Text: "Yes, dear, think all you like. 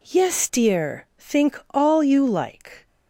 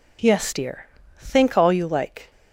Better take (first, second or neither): neither